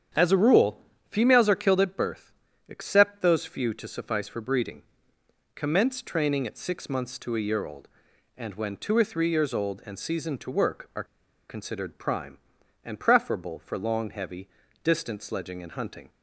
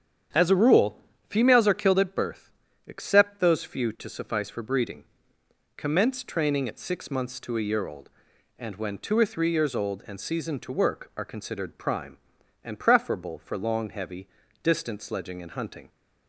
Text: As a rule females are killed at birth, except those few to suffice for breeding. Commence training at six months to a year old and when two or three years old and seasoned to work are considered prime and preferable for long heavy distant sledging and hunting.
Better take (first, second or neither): second